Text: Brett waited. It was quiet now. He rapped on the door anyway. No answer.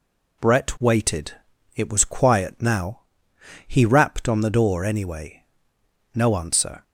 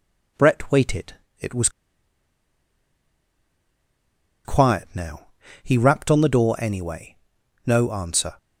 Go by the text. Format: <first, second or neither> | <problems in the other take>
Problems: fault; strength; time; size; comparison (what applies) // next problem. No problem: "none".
first | pauses between "was" and "quiet"; strong; at 1.6 s; 2.7 s long